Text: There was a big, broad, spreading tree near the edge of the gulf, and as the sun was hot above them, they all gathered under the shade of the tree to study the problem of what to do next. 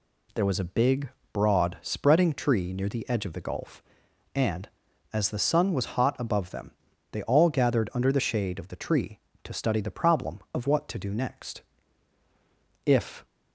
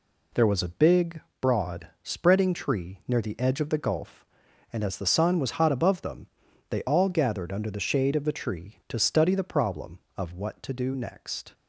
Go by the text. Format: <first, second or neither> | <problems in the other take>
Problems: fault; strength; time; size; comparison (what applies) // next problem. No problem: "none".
second | goes on to say "If"; slight; from 12.8 s on; 0.40 s long